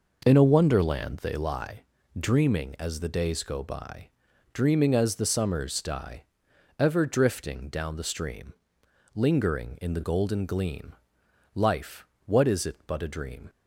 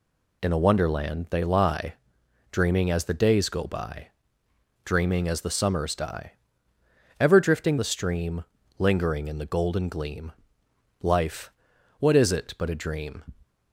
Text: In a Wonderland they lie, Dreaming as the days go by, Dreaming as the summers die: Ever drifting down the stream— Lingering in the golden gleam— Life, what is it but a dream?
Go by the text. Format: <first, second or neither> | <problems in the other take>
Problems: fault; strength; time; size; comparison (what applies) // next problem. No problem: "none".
first | skips "down"; at 7.7 s